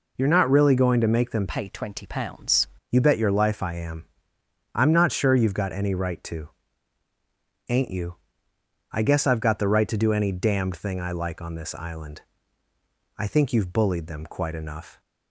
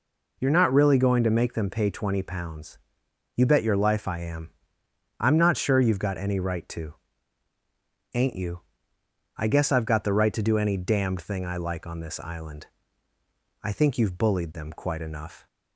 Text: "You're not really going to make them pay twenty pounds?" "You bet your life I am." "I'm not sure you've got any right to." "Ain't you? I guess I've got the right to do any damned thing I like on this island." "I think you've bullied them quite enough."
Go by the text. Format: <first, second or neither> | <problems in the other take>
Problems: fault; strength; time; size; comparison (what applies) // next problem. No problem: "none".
second | changes voice from "pay" to "pounds"; from 1.4 to 2.6 s; 1.2 s long